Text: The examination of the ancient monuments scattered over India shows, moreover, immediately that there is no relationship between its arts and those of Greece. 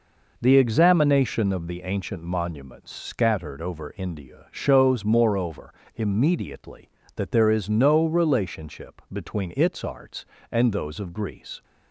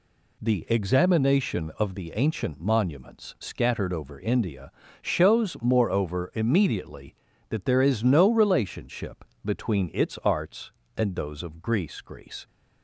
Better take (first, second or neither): first